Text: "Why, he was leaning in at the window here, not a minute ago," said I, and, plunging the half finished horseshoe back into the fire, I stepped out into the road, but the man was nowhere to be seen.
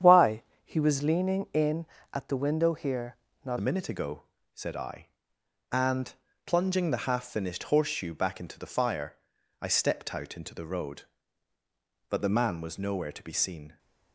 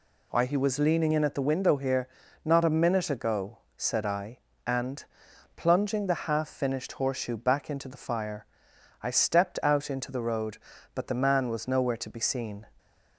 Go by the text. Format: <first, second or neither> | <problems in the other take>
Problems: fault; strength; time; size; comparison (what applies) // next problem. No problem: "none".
second | starts louder than the rest; strong; until 1.2 s; 9 dB // changes voice at "a"; from 3.5 s on; 10.2 s long